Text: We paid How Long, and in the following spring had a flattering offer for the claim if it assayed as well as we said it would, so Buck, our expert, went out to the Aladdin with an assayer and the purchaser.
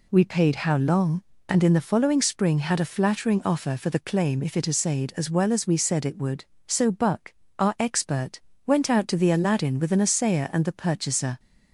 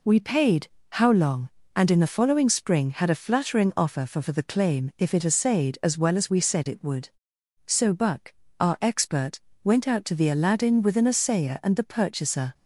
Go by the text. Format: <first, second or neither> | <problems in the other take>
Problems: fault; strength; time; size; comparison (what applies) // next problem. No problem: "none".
first | pauses between "paid" and "How"; slight; at 0.6 s; 0.26 s long // says "for" twice; at 4.1 s